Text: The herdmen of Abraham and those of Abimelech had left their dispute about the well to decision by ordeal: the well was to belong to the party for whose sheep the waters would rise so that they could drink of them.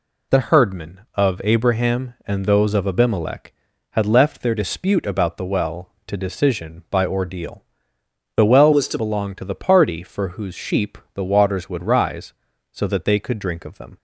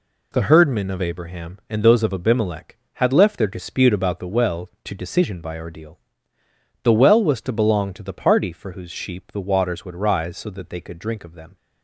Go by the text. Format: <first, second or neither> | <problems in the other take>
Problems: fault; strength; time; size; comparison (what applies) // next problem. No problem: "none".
second | changes voice from "was" to "to"; from 8.7 to 8.9 s; 0.2 s long // pauses between "sheep" and "the"; slight; at 10.9 s; 0.18 s long